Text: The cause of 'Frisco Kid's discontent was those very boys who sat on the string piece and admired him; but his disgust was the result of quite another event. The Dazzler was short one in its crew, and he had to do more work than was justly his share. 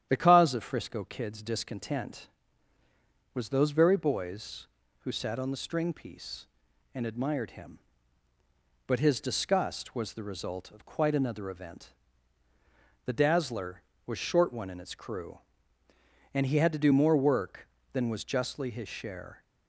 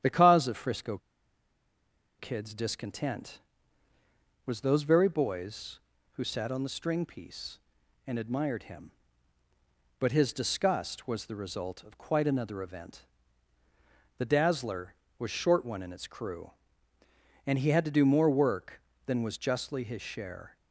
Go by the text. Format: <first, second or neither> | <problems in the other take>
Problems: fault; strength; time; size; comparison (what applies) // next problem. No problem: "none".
first | starts louder than the rest; strong; until 2.2 s; 10 dB; strong in the first // pauses between "Frisco" and "Kid's"; at 0.9 s; 1.2 s long